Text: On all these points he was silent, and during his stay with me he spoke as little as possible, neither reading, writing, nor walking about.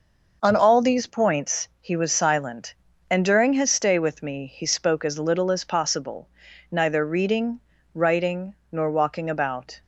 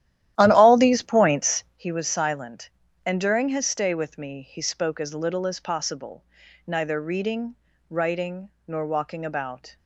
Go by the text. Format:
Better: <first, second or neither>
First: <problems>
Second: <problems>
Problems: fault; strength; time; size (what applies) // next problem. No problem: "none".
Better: first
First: none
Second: starts louder than the rest; strong; until 1.9 s; 13 dB